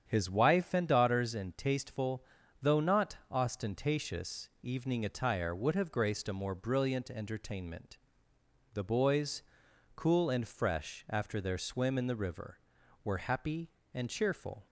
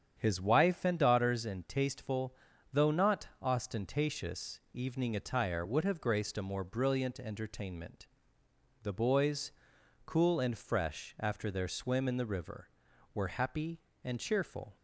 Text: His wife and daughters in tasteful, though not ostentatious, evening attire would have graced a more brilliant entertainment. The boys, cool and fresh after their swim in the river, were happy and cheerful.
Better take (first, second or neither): neither